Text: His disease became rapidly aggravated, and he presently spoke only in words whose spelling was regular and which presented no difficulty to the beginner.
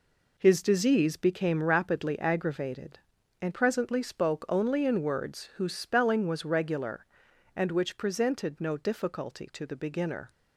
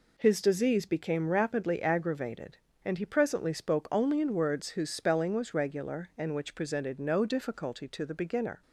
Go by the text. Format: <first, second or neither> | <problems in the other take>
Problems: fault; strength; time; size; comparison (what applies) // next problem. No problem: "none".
second | skips "he"; at 3.5 s